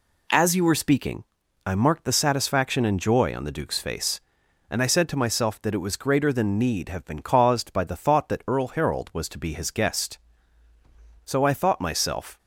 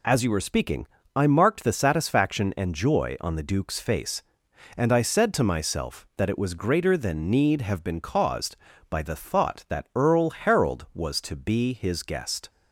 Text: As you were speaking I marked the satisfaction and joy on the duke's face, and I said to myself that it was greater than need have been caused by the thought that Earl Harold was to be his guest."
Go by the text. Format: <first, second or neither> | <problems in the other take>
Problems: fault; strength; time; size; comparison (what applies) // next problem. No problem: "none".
second | pauses between "speaking" and "I"; at 1.2 s; 0.42 s long; slight in the second // goes on to say "So I thought myself"; noticeable; from 11.2 s on; 1.1 s long